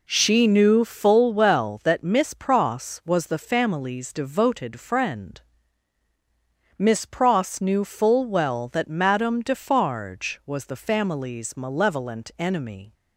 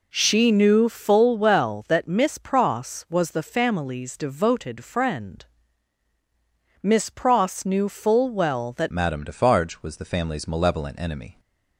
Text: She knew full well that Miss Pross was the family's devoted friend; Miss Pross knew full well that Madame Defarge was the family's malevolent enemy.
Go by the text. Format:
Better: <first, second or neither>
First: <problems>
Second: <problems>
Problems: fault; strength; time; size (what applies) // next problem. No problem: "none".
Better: first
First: none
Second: changes voice at "Madame"; from 8.9 s on; 2.4 s long